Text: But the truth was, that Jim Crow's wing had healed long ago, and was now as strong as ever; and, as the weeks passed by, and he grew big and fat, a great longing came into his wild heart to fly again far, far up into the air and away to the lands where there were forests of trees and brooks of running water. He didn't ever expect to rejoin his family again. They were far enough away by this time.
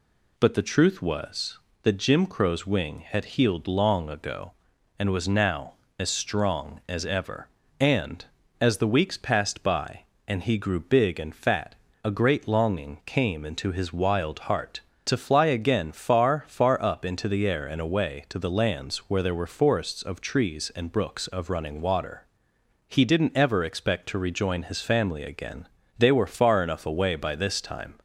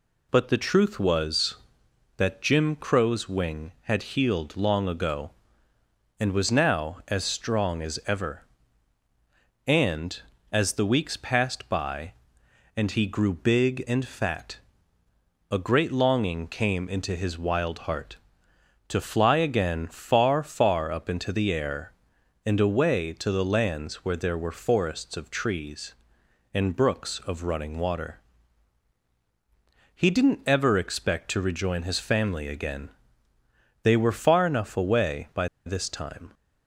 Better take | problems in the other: first | pauses between "by" and "this"; slight; at 35.4 s; 0.17 s long

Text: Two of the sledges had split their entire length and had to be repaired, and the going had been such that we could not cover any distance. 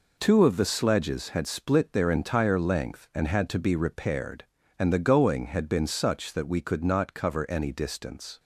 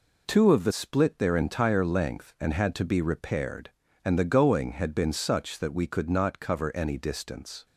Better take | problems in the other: first | skips "sledges had"; at 0.7 s

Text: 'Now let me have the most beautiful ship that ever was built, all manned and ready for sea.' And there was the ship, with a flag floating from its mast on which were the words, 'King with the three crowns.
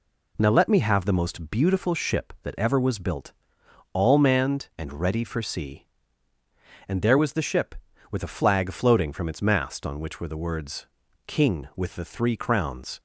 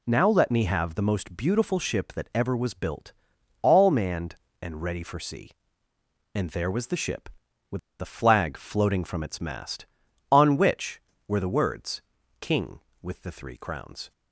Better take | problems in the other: first | pauses between "with" and "a"; slight; at 7.7 s; 0.21 s long

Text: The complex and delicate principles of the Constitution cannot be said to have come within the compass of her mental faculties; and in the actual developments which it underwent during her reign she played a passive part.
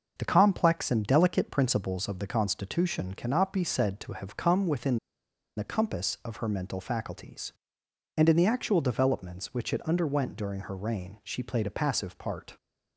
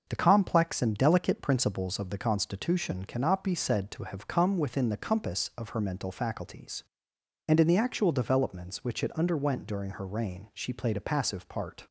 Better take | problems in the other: second | starts louder than the rest; until 1.1 s; 6 dB; also in the second // pauses between "within" and "the"; noticeable; at 4.9 s; 0.60 s long

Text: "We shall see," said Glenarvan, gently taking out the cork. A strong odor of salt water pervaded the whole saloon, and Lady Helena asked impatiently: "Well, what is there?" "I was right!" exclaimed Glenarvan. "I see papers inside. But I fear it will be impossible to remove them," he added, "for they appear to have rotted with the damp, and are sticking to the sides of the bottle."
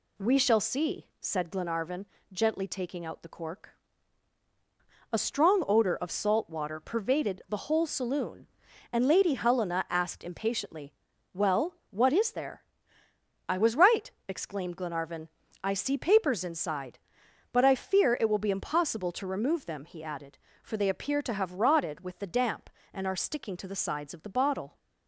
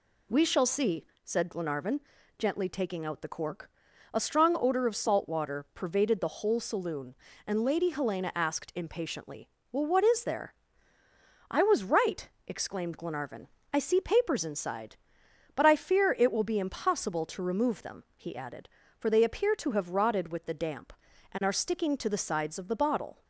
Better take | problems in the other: neither | none

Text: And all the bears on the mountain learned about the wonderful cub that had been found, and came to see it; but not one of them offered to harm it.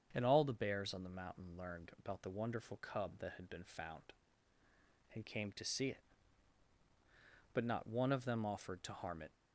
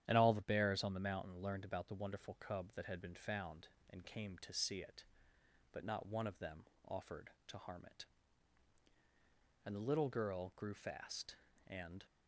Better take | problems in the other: first | starts louder than the rest; strong; until 1.0 s; 10.5 dB; also in the first // pauses between "them" and "offered"; slight; at 6.6 s; 0.24 s long // goes on to say "And the little girl grew fast and"; strong; from 9.6 s on; 2.4 s long

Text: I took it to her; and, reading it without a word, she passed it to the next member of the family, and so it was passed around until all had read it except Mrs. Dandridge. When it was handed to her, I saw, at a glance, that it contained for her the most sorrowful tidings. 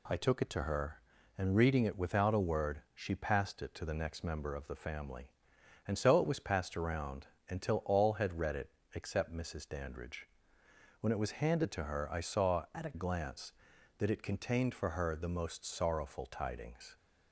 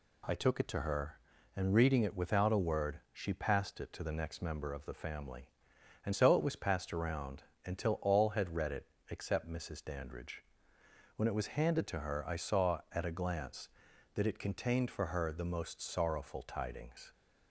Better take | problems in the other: second | pauses between "around" and "until"; slight; at 7.2 s; 0.22 s long; slight in the second // pauses between "it" and "except"; slight; at 8.7 s; 0.24 s long; slight in the second // changes voice from "at" to "a"; from 12.7 to 12.9 s; 0.2 s long

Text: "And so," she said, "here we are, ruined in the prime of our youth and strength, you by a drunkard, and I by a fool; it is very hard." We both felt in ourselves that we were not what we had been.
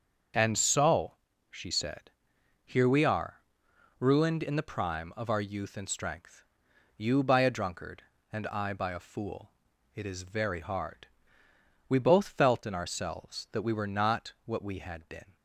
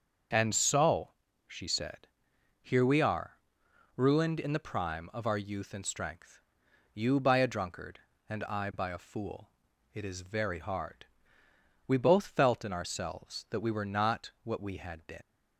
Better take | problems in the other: first | starts louder than the rest; until 1.6 s; 6.5 dB; also in the first // leaves "been" unfinished; at 15.2 s; 120 ms

